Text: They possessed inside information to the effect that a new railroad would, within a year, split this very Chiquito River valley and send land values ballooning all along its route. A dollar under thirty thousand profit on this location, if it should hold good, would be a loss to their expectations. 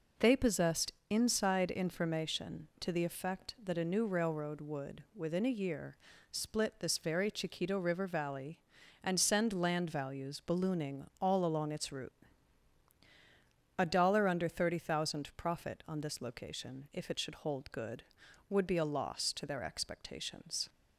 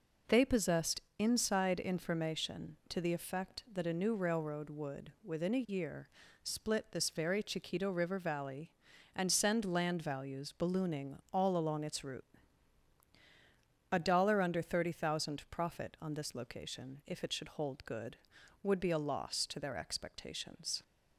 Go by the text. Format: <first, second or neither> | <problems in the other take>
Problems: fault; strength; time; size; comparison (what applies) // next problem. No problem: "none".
neither | pauses between "possessed" and "inside"; slight; the same in both // pauses between "ballooning" and "all"; slight; the same in both